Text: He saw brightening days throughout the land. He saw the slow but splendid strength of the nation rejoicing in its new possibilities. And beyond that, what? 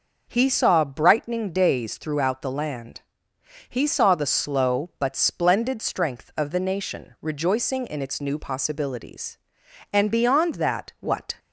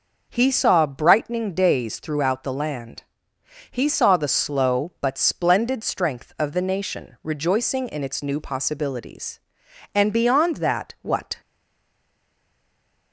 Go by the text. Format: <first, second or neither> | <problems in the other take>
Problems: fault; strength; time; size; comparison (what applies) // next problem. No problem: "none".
first | stays silent after the last word; noticeable; from 11.4 s on; 1.7 s long